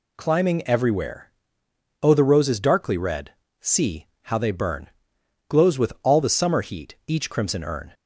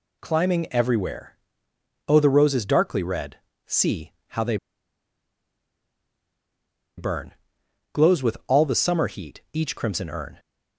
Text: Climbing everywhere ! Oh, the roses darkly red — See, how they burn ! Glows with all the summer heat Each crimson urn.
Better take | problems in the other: first | pauses between "they" and "burn"; strong; at 4.5 s; 2.4 s long

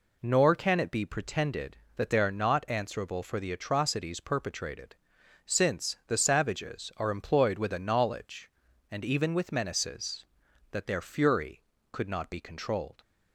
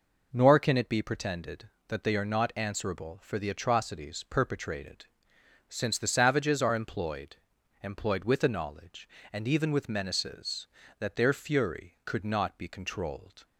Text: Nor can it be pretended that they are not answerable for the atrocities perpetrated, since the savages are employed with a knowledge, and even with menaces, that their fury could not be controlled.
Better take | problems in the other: first | says "employed" twice; at 7.8 s

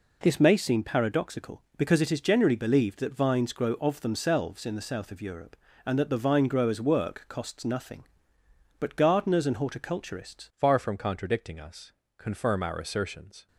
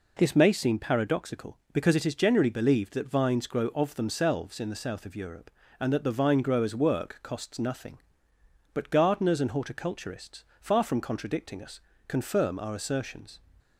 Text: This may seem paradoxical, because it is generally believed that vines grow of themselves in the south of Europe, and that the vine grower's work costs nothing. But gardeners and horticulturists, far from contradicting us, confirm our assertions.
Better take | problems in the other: second | changes voice at "far"; from 10.5 s on; 2.9 s long

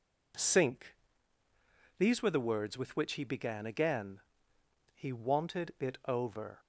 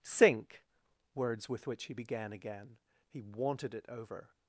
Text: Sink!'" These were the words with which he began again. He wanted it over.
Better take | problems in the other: first | skips "These were the"; at 0.8 s

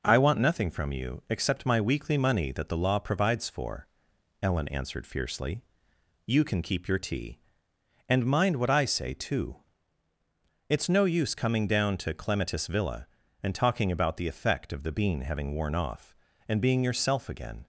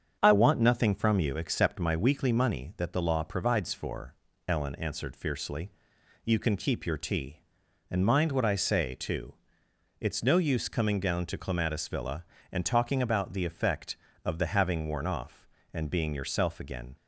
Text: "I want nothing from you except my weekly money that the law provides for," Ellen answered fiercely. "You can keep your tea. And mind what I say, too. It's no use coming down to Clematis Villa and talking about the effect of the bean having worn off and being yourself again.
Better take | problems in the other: first | starts louder than the rest; strong; until 1.2 s; 7.5 dB // skips "bean"; at 14.4 s

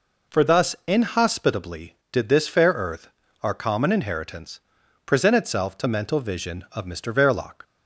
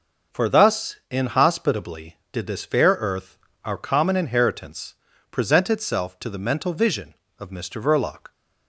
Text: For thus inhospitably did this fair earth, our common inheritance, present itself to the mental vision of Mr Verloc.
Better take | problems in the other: second | skips "the"; at 5.8 s

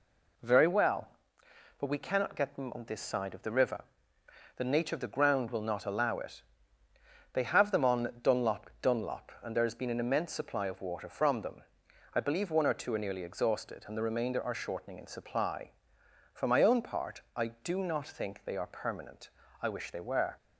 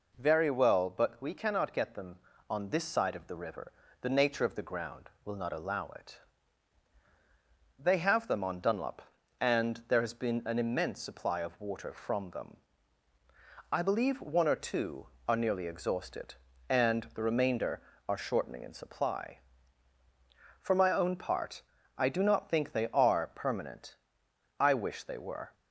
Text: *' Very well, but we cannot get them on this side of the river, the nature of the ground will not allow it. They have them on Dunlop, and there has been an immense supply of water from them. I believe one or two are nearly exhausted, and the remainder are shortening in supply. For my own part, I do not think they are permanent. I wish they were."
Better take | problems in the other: second | says "Dunlop" twice; at 8.8 s

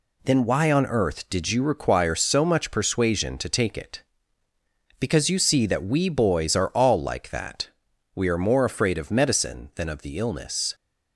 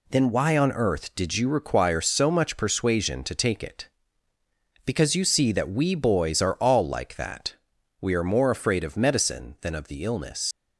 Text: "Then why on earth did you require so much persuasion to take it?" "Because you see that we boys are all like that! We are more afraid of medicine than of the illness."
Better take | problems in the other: first | leaves "illness" unfinished; at 10.5 s; 95 ms

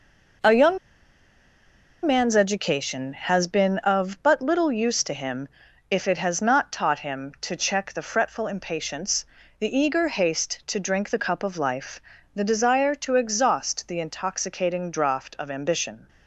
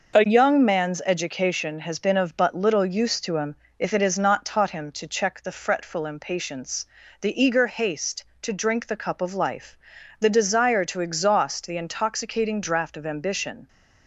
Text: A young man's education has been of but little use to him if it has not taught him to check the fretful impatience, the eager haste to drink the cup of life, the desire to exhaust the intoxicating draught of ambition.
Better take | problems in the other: second | pauses between "young" and "man's"; strong; at 0.7 s; 1.2 s long // pauses between "him" and "if"; at 5.4 s; 0.42 s long; slight in the second

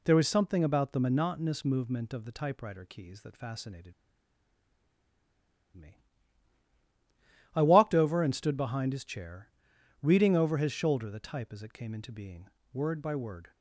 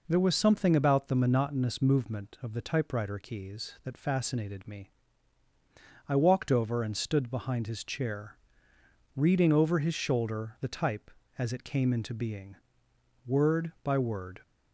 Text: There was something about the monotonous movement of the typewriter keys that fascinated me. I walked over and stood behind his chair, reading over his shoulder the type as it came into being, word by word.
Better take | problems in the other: second | pauses between "fascinated" and "me"; strong; at 3.9 s; 1.8 s long

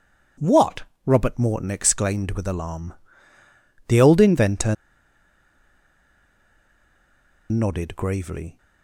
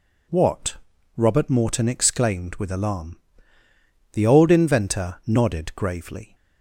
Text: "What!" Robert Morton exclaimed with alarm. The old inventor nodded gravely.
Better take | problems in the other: second | pauses between "inventor" and "nodded"; strong; at 4.7 s; 2.7 s long

